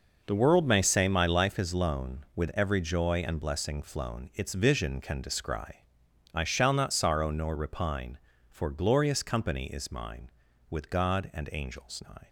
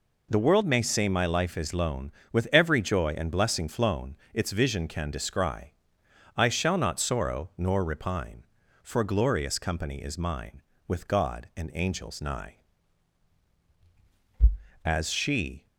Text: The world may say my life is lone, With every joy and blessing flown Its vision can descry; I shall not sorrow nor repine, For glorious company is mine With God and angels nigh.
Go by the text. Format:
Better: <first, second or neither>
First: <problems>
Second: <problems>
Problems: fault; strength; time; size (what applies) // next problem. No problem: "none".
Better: first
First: none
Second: pauses between "flown" and "Its"; slight; at 4.1 s; 0.18 s long // goes on to say "As she"; noticeable; from 14.8 s on; 0.82 s long